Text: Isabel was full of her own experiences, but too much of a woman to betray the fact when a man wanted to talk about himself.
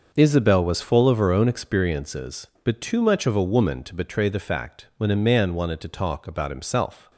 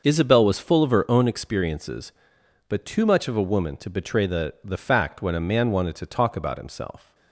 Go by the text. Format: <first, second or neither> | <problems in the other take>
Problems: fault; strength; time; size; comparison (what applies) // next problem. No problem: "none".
first | starts louder than the rest; until 1.0 s; 6 dB; noticeable in the first // says "the" twice; at 4.6 s